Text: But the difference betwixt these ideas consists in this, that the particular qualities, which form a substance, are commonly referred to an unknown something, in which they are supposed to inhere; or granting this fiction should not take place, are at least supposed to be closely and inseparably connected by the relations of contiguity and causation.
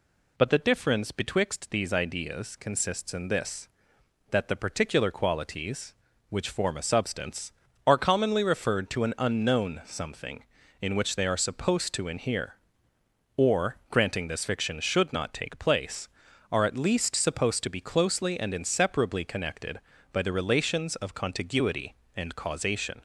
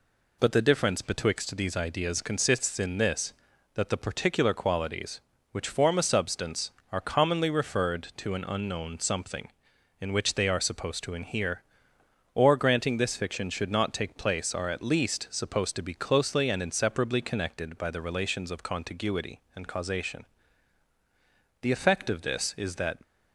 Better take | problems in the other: first | goes on to say "The effect of this is that"; from 21.6 s on; 1.3 s long

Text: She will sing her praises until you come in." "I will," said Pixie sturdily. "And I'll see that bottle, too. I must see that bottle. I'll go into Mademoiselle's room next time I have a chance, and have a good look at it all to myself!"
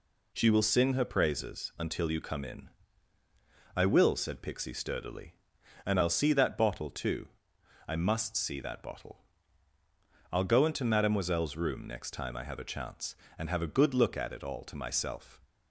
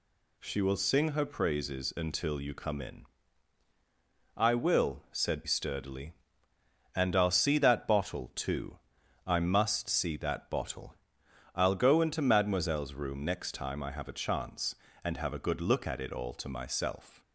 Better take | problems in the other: first | skips "Pixie"; at 5.4 s

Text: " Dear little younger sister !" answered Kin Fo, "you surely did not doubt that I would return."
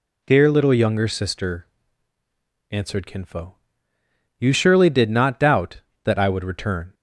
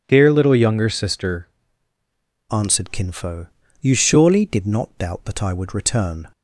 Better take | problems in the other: first | changes voice at "answered"; from 2.5 s on; 3.7 s long

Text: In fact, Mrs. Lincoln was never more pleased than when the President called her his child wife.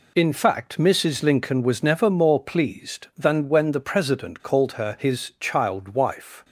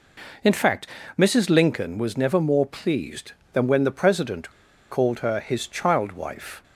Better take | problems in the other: first | pauses between "President" and "called"; at 4.5 s; 0.40 s long

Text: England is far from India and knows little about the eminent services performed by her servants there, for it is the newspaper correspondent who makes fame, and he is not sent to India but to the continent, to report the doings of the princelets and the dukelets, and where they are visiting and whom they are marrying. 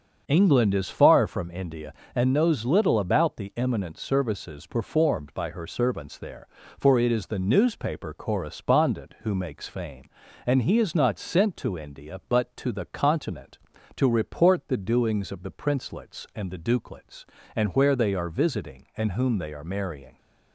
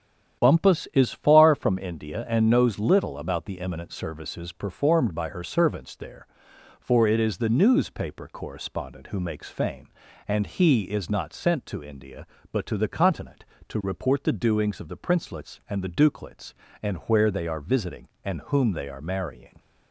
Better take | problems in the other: first | starts louder than the rest; strong; until 1.4 s; 9.5 dB; also in the first // says "Bumpus" for "England"; at 0.4 s

